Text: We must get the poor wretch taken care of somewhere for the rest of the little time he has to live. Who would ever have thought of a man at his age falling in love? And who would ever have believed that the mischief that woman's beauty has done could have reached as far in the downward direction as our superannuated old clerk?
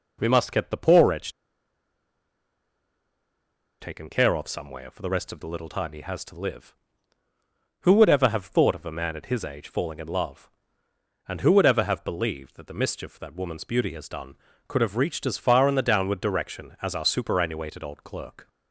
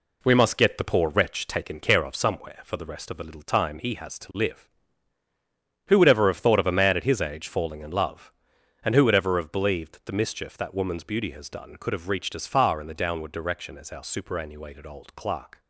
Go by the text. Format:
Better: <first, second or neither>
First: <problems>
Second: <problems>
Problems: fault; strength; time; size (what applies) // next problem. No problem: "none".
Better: second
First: pauses between "wretch" and "taken"; strong; at 1.3 s; 2.4 s long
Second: none